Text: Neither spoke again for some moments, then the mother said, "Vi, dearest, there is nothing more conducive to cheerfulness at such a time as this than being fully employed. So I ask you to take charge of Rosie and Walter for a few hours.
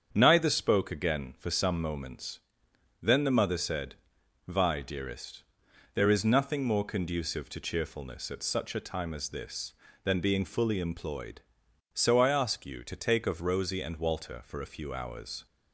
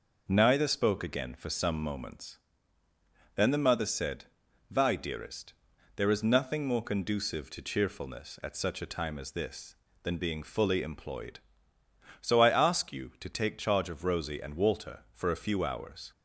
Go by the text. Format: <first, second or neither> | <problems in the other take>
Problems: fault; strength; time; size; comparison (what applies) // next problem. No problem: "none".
second | starts louder than the rest; strong; until 1.1 s; 7.5 dB // skips "charge"; at 13.2 s